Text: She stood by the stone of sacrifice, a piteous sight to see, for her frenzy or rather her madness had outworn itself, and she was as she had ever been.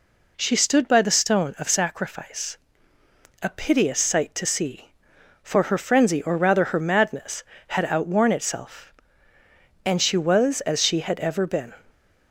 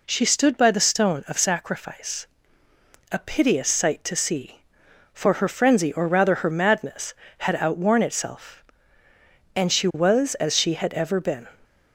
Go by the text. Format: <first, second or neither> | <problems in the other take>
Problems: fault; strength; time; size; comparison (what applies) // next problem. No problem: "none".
neither | none